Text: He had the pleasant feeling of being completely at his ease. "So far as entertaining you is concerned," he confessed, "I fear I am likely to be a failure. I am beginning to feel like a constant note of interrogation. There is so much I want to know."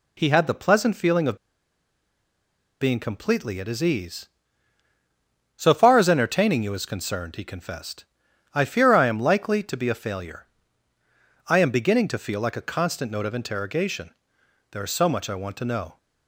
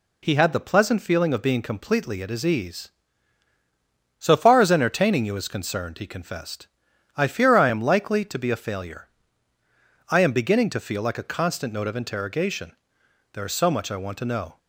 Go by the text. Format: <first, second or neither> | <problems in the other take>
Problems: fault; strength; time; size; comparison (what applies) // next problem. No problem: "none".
second | pauses between "of" and "being"; strong; at 1.3 s; 1.4 s long